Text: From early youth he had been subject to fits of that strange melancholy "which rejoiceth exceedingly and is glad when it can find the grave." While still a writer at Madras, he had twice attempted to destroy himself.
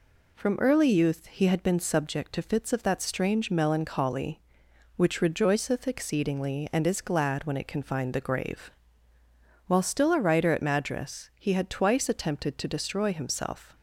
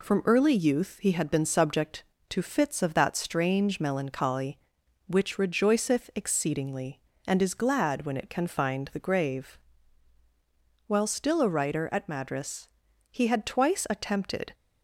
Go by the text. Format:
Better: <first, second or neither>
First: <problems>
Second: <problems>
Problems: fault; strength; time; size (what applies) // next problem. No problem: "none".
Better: first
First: none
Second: stops before "to destroy himself"; at 14.5 s